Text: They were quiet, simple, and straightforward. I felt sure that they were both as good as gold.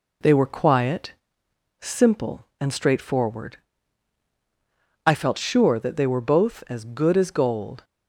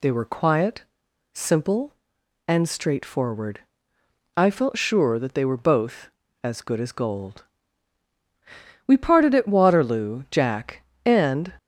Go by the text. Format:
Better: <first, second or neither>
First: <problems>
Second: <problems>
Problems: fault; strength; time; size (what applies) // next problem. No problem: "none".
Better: first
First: none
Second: goes on to say "We parted at Waterloo Jack and"; strong; from 8.8 s on; 2.6 s long